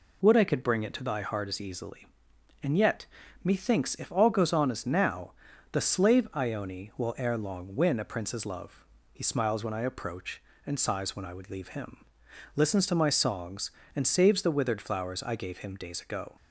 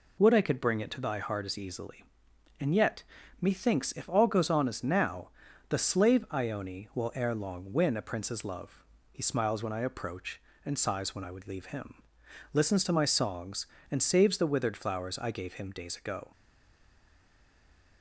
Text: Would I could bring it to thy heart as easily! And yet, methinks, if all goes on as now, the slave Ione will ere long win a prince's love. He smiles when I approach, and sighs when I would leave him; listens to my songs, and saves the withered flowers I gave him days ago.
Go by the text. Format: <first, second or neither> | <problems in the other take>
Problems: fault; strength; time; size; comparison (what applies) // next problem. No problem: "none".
first | stays silent after the last word; noticeable; from 16.3 s on; 1.7 s long